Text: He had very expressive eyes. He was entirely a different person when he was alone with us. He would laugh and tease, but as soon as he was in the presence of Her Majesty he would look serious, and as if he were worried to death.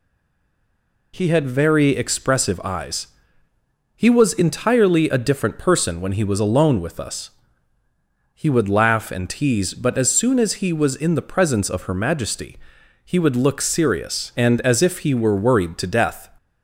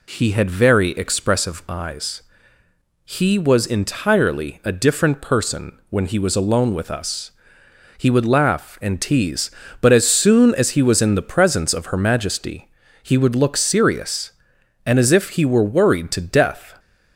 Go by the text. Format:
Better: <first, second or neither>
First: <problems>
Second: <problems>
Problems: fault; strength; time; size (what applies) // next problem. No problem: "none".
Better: second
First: stays silent before the first word; until 1.1 s; 1.1 s long // pauses between "Majesty" and "he"; noticeable; at 12.5 s; 0.48 s long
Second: pauses between "Majesty" and "he"; slight; at 12.6 s; 0.34 s long